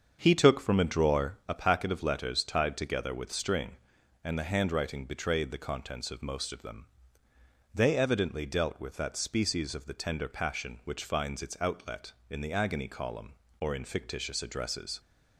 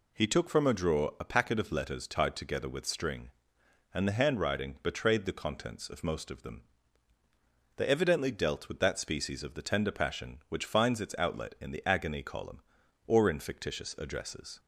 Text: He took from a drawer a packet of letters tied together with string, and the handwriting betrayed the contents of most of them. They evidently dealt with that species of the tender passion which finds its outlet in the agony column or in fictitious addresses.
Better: second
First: starts louder than the rest; until 1.7 s; 7 dB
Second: none

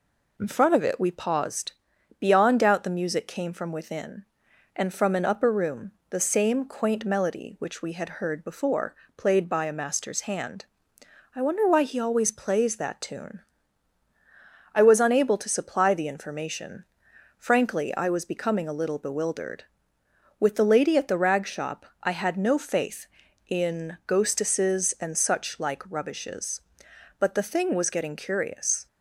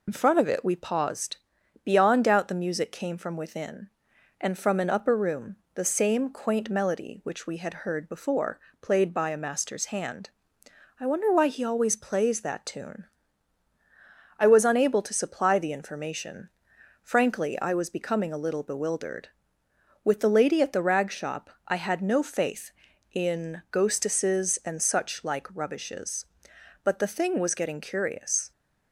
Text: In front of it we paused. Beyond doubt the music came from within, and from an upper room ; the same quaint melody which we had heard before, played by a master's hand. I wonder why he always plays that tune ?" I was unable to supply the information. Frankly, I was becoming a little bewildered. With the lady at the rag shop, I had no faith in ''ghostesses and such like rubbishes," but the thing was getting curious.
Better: first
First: none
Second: loses the start of "In"; at 0.0 s; 40 ms

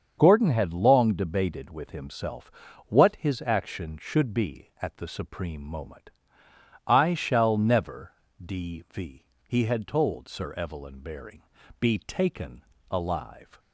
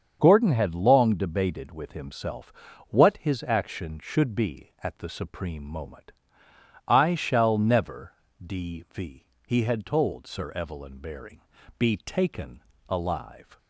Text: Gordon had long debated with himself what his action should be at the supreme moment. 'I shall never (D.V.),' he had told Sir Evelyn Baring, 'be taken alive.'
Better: neither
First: starts louder than the rest; until 1.1 s; 7 dB // pauses between "himself" and "what"; slight; at 2.5 s; 0.36 s long // pauses between "taken" and "alive"; slight; at 12.6 s; 0.28 s long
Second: starts louder than the rest; until 1.2 s; 7 dB // pauses between "himself" and "what"; slight; at 2.5 s; 0.36 s long // pauses between "taken" and "alive"; slight; at 12.6 s; 0.28 s long

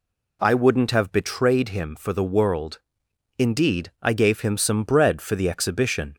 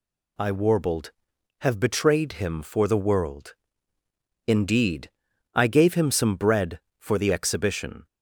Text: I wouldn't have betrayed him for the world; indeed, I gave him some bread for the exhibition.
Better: first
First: none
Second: says "warbled" for "wouldn't"; at 0.5 s

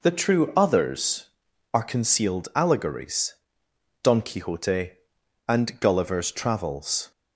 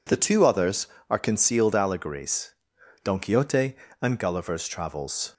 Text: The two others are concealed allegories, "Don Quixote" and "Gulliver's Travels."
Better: second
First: says "true" for "two"; at 0.1 s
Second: none

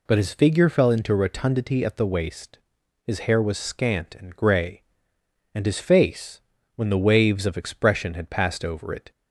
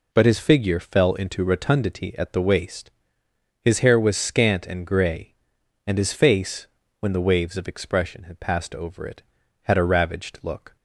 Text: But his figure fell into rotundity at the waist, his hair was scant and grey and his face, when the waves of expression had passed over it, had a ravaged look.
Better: second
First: stops before "had a ravaged look"; at 9.1 s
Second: none

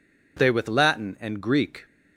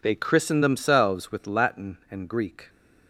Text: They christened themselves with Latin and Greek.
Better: second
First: skips "christened themselves"; at 0.5 s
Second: none

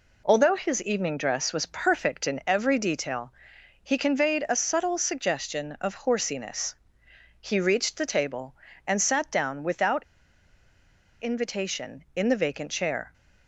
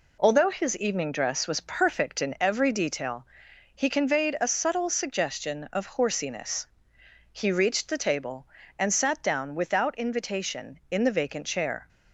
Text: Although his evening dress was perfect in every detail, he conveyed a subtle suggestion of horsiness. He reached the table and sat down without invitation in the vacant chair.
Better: second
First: pauses between "without" and "invitation"; at 10.0 s; 1.1 s long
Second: none

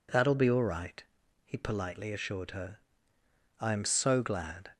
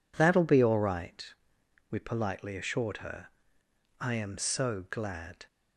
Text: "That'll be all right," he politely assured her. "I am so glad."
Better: first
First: none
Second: says "we" for "he"; at 1.9 s

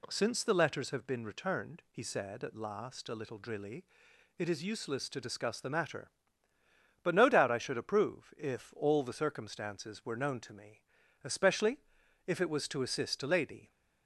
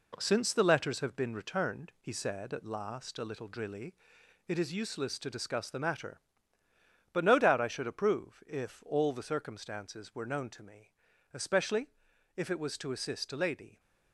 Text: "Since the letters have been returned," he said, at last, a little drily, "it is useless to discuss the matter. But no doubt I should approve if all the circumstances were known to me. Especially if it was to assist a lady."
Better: first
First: pauses between "Especially" and "if"; noticeable; at 11.8 s; 0.46 s long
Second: gets quieter; noticeable; throughout; 4.5 dB // pauses between "Especially" and "if"; noticeable; at 11.8 s; 0.46 s long

